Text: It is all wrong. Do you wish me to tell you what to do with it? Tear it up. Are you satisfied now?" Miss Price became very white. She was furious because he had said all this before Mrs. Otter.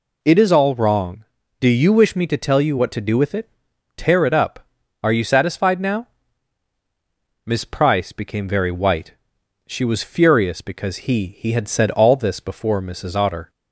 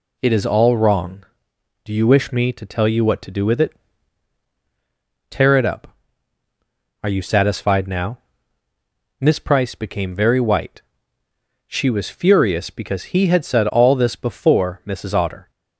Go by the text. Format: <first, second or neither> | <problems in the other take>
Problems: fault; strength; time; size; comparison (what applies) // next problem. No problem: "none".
second | says "he" twice; at 11.3 s